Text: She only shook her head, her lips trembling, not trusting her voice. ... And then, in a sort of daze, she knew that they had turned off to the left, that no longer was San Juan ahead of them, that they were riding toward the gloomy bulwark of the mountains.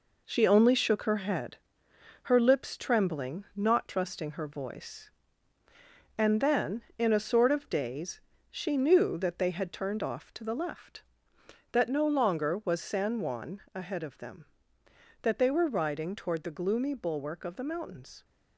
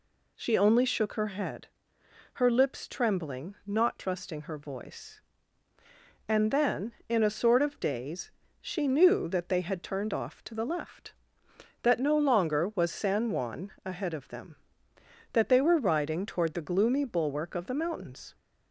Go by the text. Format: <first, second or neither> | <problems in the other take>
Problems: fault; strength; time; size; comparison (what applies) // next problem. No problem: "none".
second | gets quieter; throughout; 6.5 dB